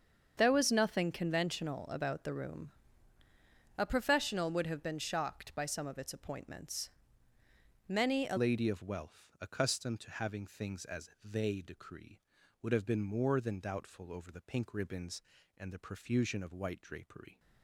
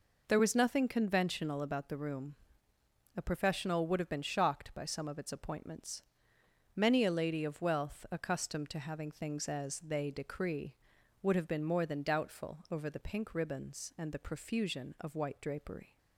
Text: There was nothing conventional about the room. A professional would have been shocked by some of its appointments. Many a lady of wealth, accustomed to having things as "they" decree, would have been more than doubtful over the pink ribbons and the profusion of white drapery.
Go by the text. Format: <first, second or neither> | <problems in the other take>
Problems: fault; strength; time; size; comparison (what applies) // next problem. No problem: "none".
second | starts louder than the rest; strong; until 1.3 s; 7 dB // changes voice at "lady"; from 8.3 s on; 9.0 s long